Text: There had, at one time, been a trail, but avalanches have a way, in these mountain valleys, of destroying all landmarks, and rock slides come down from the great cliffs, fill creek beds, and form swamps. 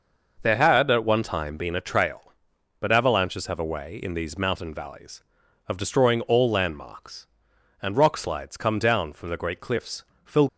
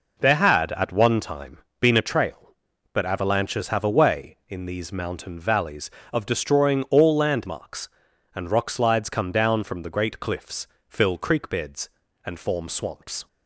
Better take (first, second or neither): second